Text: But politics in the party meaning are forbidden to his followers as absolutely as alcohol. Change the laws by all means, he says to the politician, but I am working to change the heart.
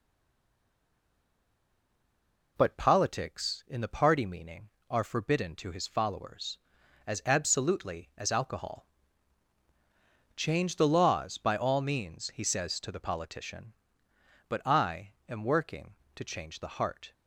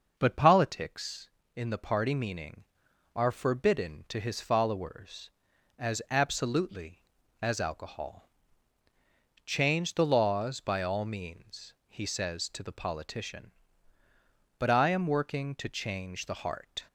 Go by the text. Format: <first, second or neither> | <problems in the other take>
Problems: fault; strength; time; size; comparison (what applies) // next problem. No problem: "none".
second | stays silent before the first word; strong; until 2.5 s; 2.5 s long // pauses between "I" and "am"; slight; at 15.1 s; 0.16 s long